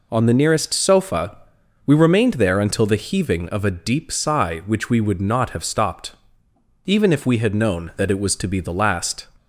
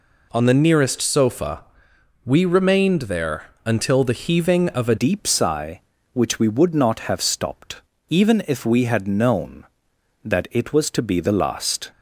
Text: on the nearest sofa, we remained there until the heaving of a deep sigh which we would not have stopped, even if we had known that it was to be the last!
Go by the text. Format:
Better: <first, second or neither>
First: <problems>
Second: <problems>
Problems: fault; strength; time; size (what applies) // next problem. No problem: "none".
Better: first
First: none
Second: pauses between "there" and "until"; slight; at 3.4 s; 0.20 s long // changes voice at "deep"; from 4.9 s on; 6.9 s long